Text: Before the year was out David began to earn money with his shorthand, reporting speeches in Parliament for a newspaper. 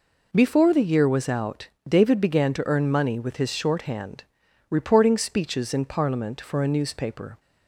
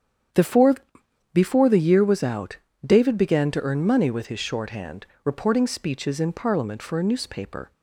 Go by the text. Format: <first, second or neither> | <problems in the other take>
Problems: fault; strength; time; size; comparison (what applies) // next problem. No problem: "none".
first | starts louder than the rest; strong; until 1.9 s; 8.5 dB // says "Before" twice; at 1.3 s // pauses between "out" and "David"; slight; at 2.5 s; 0.30 s long; slight in the first